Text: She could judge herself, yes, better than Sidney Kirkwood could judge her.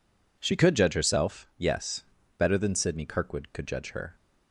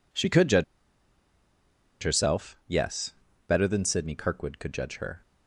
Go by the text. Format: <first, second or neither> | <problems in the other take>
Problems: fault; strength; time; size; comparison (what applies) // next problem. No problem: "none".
first | pauses between "judge" and "herself"; strong; at 0.6 s; 1.3 s long